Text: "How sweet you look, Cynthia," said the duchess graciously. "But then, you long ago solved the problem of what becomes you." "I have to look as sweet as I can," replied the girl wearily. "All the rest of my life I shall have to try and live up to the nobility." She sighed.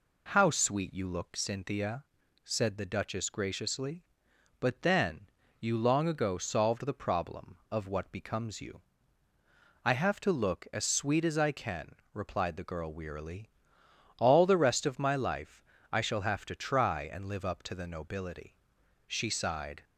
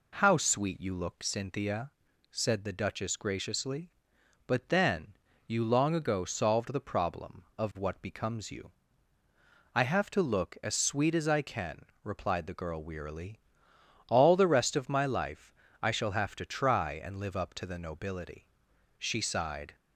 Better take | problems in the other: neither | pauses between "life" and "I"; slight; the same in both

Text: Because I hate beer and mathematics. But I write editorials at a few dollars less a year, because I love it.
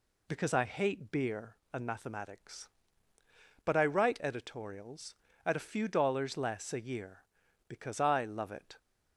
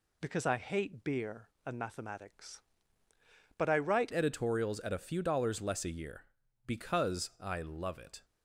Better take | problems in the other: first | changes voice at "editorials"; from 4.1 s on; 4.1 s long

